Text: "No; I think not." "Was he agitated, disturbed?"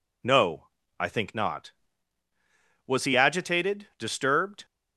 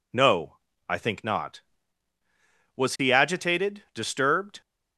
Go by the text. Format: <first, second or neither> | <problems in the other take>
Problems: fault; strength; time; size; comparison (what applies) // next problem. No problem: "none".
neither | none